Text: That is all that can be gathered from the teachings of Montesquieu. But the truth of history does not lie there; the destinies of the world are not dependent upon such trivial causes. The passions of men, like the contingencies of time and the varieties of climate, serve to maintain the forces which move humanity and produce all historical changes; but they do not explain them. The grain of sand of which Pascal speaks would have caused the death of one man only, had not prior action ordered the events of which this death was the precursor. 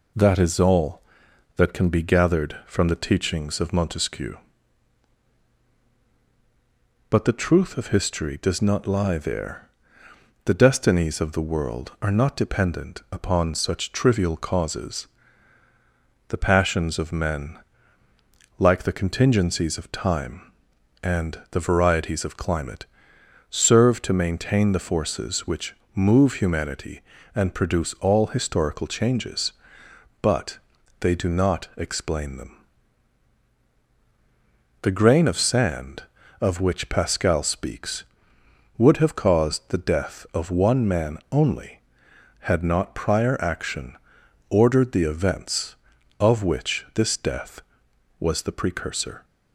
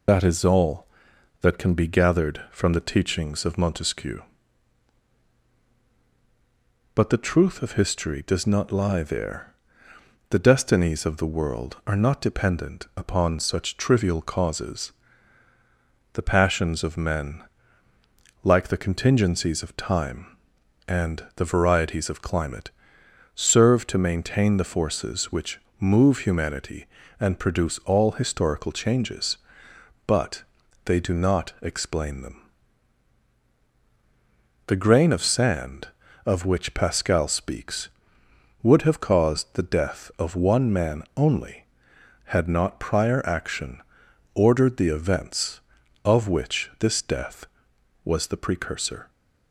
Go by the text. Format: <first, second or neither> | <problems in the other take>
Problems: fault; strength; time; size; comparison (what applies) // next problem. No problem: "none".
first | loses the start of "That"; at 0.0 s; 80 ms // pauses between "which" and "move"; slight; at 25.5 s; 0.18 s long; slight in the first // pauses between "but" and "they"; at 30.4 s; 0.42 s long; also in the first // pauses between "action" and "ordered"; noticeable; at 43.8 s; 0.52 s long; noticeable in the first